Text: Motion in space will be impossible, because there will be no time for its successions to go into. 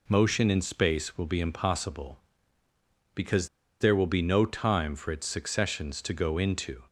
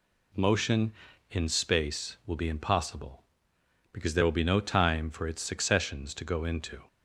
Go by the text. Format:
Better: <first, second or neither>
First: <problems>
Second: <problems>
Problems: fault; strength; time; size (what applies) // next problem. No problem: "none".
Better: second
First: pauses between "because" and "there"; slight; at 3.4 s; 0.32 s long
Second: none